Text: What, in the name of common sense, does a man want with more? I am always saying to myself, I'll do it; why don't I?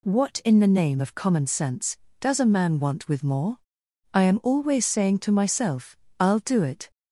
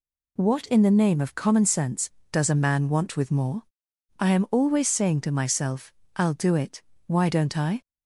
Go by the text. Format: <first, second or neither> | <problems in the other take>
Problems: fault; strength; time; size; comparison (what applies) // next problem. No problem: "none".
second | stops before "why don't I"; at 6.9 s